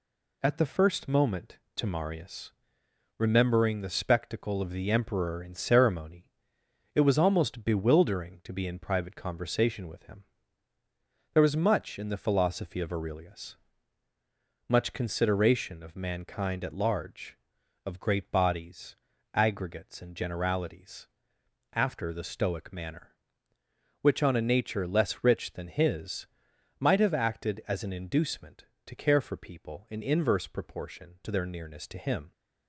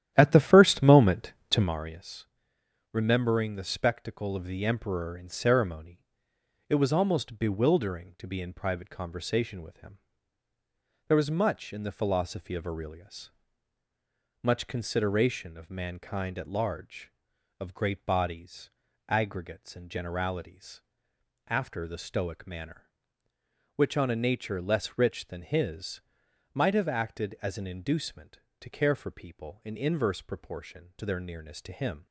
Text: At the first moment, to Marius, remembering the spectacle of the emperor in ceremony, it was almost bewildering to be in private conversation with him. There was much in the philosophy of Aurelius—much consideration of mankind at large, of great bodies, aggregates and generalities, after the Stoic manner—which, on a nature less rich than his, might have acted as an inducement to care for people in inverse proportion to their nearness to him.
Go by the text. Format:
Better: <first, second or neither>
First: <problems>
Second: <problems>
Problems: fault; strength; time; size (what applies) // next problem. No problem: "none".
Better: first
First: none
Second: starts louder than the rest; strong; until 1.8 s; 11.5 dB